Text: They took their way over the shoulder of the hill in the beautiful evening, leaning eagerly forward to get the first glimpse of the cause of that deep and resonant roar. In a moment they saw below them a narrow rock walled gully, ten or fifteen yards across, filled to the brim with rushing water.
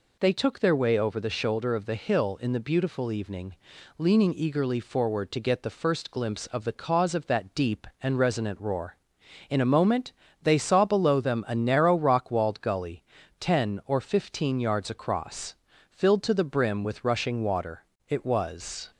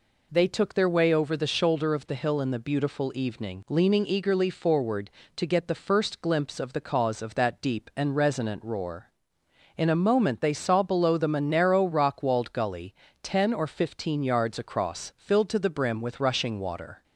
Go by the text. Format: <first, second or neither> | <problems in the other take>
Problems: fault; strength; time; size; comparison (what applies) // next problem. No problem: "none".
second | pauses between "moment" and "they"; slight; at 10.1 s; 0.30 s long // goes on to say "It was"; noticeable; from 18.0 s on; 0.80 s long